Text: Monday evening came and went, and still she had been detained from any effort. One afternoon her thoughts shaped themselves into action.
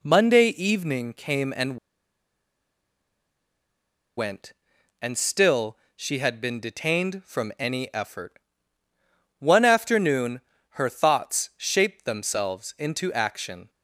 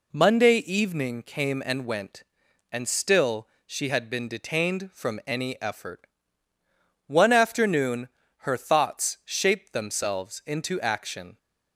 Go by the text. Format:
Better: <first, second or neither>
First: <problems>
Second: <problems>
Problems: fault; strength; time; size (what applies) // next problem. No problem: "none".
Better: second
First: pauses between "and" and "went"; strong; at 1.7 s; 2.4 s long // pauses between "still" and "she"; slight; at 5.7 s; 0.18 s long // pauses between "afternoon" and "her"; slight; at 10.3 s; 0.34 s long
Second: pauses between "still" and "she"; slight; at 3.4 s; 0.18 s long // pauses between "afternoon" and "her"; slight; at 8.0 s; 0.34 s long